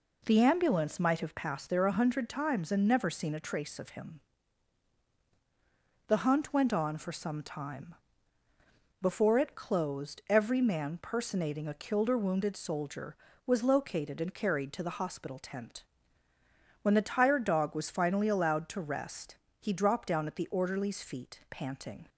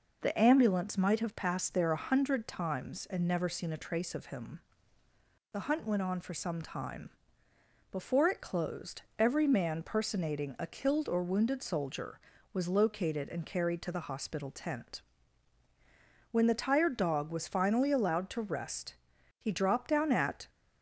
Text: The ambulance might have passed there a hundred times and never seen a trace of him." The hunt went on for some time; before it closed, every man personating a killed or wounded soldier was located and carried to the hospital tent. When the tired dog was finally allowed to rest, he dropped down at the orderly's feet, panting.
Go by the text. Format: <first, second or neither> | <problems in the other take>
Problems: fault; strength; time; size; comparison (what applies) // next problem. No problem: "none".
first | stops before "the orderly's feet panting"; at 20.4 s